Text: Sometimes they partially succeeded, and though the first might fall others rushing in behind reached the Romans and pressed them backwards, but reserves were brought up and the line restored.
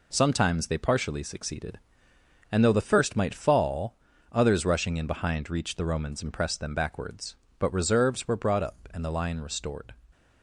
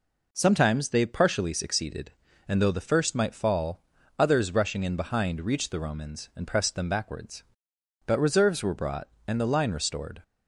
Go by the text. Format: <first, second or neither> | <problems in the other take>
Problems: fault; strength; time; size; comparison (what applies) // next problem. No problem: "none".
first | pauses between "fall" and "others"; slight; at 3.8 s; 0.34 s long; slight in the first // skips "up"; at 9.1 s